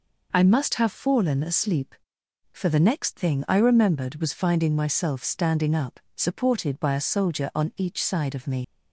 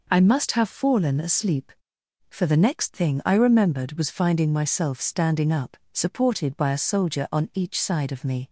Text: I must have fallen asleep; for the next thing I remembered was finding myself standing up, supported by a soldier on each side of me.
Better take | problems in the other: second | leaves "me" unfinished; at 8.6 s; 65 ms

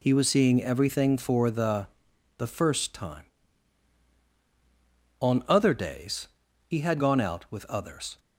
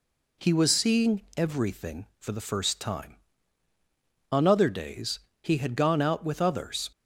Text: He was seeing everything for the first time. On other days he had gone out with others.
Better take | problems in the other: second | says "the" twice; at 2.3 s // pauses between "days" and "he"; at 6.2 s; 0.38 s long; slight in the second

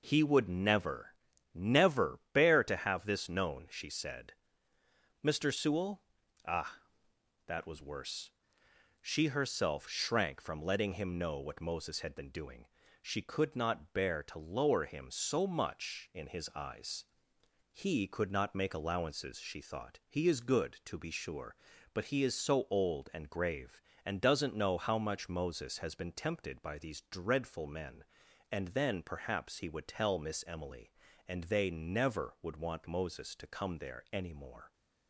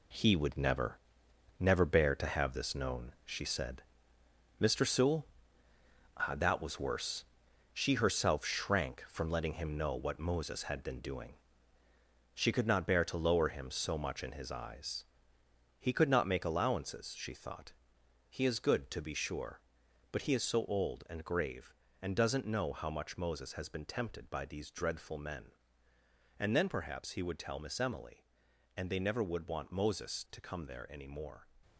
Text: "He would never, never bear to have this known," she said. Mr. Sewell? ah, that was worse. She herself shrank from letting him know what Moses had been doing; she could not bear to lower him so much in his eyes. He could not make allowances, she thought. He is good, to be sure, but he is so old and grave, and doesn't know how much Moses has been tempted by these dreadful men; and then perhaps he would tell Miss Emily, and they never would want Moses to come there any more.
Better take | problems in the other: first | gets quieter; strong; throughout; 8.5 dB

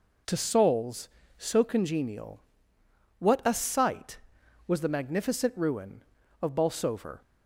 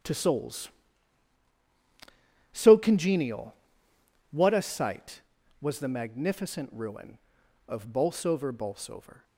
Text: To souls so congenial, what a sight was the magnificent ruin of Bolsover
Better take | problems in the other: first | starts louder than the rest; strong; until 2.8 s; 10 dB // says "Bolsover" twice; at 8.5 s

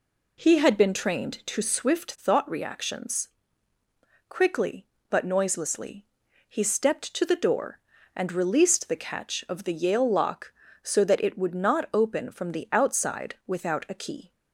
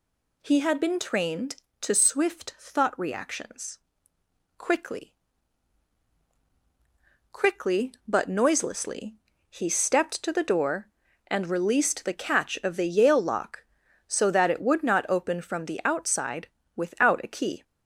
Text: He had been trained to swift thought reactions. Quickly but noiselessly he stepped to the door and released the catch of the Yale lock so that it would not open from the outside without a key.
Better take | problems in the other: first | says "Quickly" twice; at 7.3 s // pauses between "noiselessly" and "he"; slight; at 9.1 s; 0.32 s long; also in the first // pauses between "outside" and "without"; slight; at 16.4 s; 0.26 s long

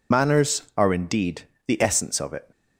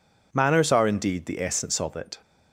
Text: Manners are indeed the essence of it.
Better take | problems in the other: second | loses the start of "Manners"; at 0.1 s; 85 ms // pauses between "indeed" and "the"; slight; at 1.4 s; 0.24 s long

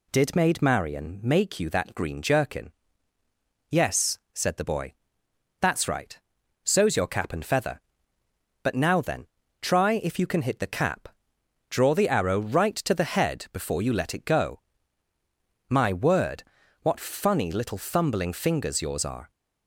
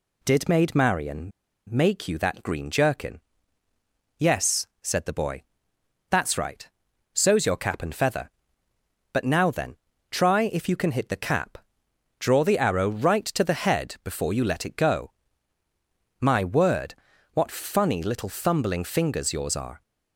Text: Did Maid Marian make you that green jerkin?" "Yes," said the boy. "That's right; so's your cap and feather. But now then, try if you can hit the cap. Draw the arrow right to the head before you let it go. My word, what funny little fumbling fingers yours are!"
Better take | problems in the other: first | pauses between "Marian" and "make"; at 1.3 s; 0.37 s long

